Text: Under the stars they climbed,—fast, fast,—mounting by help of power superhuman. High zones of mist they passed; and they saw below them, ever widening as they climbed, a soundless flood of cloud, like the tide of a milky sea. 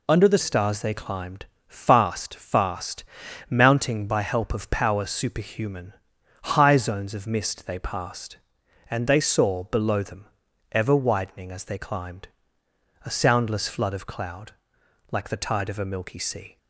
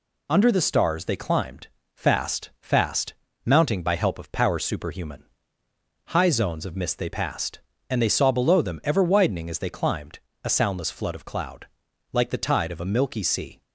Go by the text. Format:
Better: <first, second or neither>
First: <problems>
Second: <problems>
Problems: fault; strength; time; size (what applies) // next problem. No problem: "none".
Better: second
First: changes voice at "stars"; from 0.3 s on; 16.2 s long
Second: none